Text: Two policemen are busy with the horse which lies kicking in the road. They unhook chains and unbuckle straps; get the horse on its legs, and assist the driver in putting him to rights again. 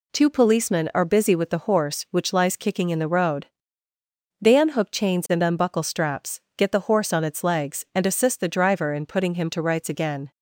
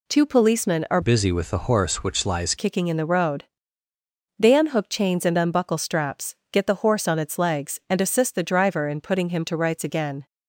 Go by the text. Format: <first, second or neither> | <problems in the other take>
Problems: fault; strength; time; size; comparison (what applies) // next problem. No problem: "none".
first | changes voice from "busy" to "lies"; from 1.0 to 2.5 s; 1.5 s long